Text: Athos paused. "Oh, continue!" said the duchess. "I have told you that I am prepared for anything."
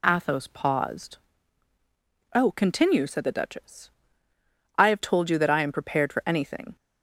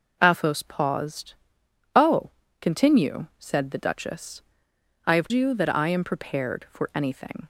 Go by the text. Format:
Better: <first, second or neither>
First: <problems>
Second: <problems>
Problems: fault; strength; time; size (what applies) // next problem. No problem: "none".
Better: first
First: none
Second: skips "told"; at 5.2 s